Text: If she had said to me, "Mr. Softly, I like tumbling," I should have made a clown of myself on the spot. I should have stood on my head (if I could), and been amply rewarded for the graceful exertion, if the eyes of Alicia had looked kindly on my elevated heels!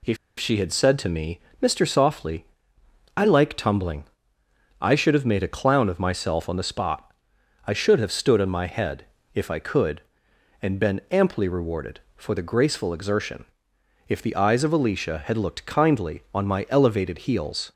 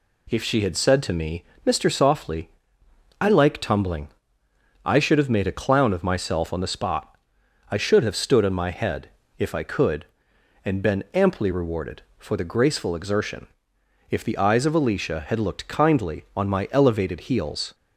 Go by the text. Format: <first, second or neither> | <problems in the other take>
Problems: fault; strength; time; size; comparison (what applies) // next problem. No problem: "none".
second | pauses between "If" and "she"; slight; at 0.1 s; 0.21 s long